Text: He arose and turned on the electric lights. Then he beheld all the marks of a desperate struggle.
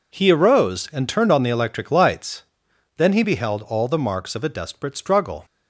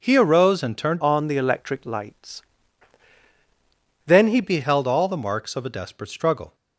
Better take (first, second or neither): first